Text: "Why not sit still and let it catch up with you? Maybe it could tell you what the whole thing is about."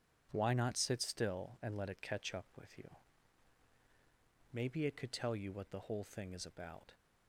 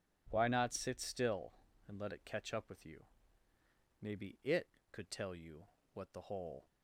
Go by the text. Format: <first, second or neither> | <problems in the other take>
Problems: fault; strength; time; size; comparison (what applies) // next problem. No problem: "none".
first | pauses between "you" and "what"; slight; at 5.6 s; 0.26 s long // stops before "thing is about"; at 6.6 s